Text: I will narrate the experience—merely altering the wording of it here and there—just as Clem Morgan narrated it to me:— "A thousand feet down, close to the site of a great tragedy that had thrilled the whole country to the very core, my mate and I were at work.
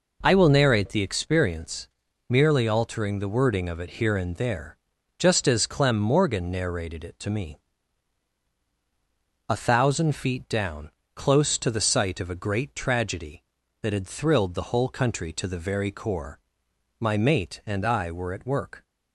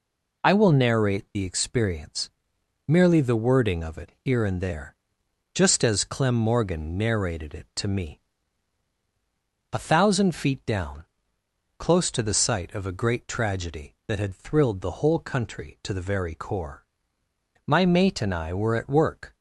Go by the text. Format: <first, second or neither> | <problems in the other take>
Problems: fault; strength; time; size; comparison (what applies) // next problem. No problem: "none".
first | skips "altering"; at 3.1 s